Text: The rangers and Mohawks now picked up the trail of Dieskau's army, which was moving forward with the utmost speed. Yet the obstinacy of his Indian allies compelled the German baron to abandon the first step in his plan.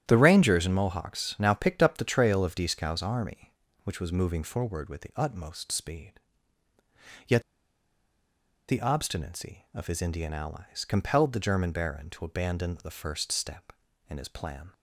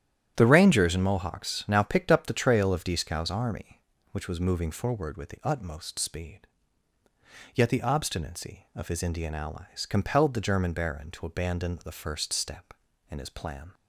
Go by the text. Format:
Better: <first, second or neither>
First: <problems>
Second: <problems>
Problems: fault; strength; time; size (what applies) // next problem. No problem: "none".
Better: second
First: starts louder than the rest; strong; until 1.0 s; 10.5 dB // pauses between "Yet" and "the"; strong; at 7.4 s; 1.2 s long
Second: starts louder than the rest; strong; until 1.3 s; 10.5 dB